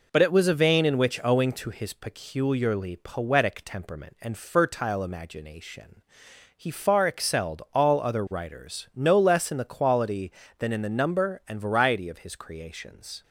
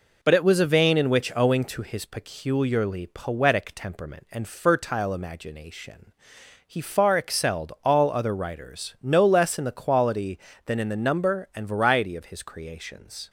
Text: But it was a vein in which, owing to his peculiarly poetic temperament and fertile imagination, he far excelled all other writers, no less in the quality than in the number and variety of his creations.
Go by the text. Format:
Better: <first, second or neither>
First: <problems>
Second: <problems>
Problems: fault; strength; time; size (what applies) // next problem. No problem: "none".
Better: neither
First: none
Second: none